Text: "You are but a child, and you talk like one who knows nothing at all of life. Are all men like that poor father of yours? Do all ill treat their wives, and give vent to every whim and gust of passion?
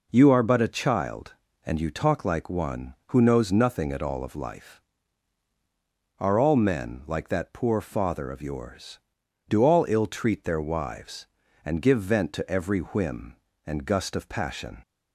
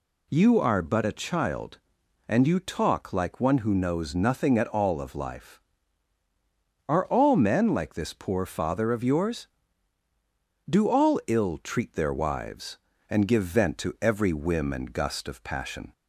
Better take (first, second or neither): first